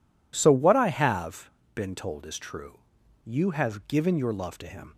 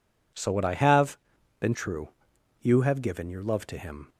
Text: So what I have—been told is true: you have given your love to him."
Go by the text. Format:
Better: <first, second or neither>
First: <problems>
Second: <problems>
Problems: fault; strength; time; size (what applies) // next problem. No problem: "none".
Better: first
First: none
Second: skips "told is"; at 1.7 s